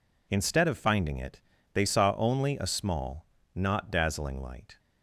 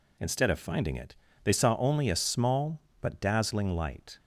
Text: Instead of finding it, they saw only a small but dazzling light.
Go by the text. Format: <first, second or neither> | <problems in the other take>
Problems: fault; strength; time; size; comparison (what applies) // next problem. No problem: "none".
second | says "not" for "but"; at 3.5 s